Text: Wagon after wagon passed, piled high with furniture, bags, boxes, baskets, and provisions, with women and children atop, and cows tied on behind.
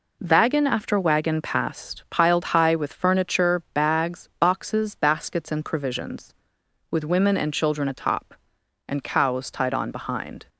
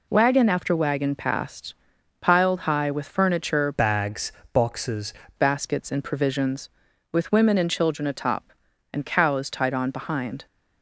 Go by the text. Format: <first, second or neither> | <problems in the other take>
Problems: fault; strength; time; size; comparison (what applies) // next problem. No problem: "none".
first | changes voice from "bags" to "boxes"; from 3.7 to 5.1 s; 1.4 s long